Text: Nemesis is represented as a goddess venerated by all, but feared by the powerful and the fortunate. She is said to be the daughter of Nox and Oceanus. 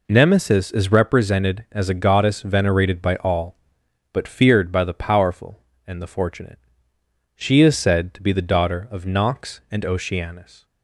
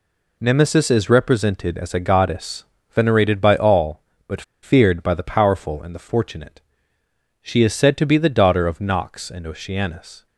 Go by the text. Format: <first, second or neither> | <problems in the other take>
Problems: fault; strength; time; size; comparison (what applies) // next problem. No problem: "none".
first | pauses between "goddess" and "venerated"; slight; at 2.6 s; 0.28 s long // pauses between "but" and "feared"; slight; at 4.4 s; 0.21 s long